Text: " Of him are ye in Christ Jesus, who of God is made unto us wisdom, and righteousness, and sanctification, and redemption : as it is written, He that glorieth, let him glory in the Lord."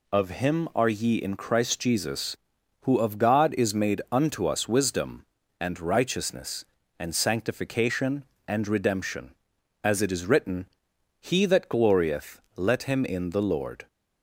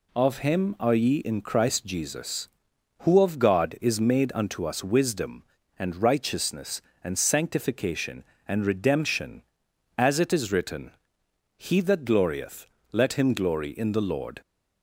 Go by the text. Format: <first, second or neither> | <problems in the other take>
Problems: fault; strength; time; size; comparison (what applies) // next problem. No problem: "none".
second | skips "glory"; at 13.0 s